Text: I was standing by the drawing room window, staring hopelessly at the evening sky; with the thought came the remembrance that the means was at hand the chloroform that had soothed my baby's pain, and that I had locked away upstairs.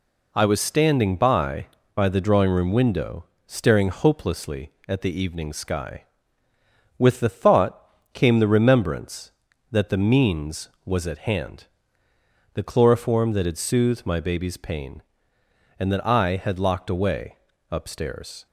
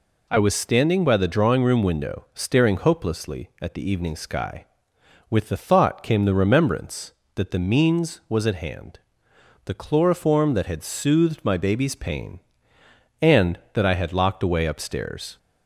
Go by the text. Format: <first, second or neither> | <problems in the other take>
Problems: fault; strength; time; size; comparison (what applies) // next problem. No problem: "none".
second | says "by" twice; at 1.9 s // pauses between "thought" and "came"; slight; at 7.9 s; 0.18 s long // pauses between "hand" and "the"; noticeable; at 11.6 s; 0.88 s long; noticeable in the second // pauses between "away" and "upstairs"; slight; at 17.3 s; 0.34 s long